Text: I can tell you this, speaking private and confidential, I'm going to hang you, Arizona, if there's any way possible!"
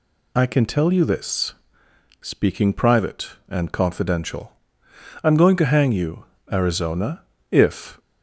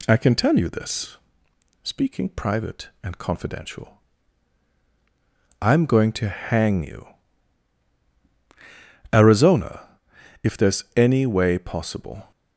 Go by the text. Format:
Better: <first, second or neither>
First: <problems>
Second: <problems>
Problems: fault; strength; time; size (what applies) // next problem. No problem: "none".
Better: second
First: stops before "there's any way possible"; at 7.9 s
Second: none